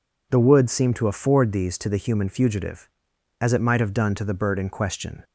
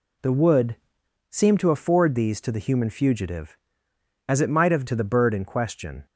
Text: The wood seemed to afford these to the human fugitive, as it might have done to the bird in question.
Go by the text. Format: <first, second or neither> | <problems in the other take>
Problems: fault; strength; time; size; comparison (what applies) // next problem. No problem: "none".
first | pauses between "wood" and "seemed"; noticeable; at 0.7 s; 0.56 s long // skips "done"; at 4.8 s